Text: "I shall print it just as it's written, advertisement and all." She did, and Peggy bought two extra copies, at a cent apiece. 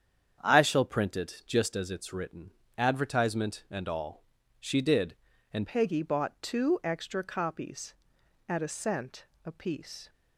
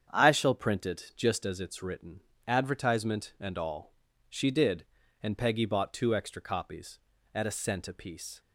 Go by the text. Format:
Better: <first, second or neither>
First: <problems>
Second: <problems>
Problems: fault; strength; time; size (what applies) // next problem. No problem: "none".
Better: second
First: starts louder than the rest; strong; until 1.4 s; 8 dB // changes voice at "Peggy"; from 5.6 s on; 4.4 s long // pauses between "cent" and "apiece"; slight; at 9.2 s; 0.20 s long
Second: starts louder than the rest; strong; until 1.1 s; 8 dB